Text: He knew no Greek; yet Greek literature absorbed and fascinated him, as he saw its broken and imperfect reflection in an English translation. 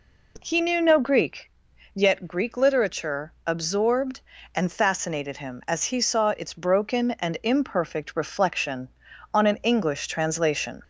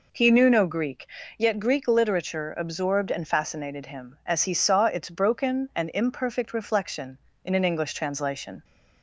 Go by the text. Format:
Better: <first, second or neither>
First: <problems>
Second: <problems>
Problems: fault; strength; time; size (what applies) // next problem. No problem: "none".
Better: second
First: says "on" for "in"; at 9.3 s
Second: none